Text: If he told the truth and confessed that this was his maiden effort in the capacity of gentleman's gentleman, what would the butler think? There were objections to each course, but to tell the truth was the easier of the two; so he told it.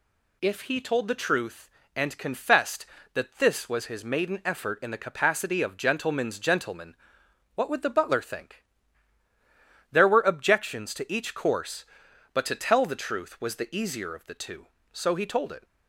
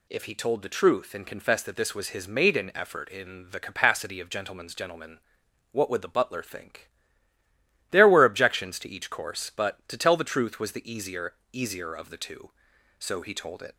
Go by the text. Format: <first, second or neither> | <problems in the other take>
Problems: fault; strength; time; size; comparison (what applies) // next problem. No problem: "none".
first | says "easier" twice; at 11.5 s